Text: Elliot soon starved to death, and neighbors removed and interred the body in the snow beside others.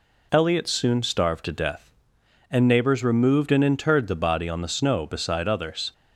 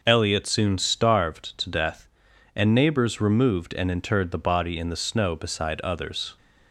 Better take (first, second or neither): second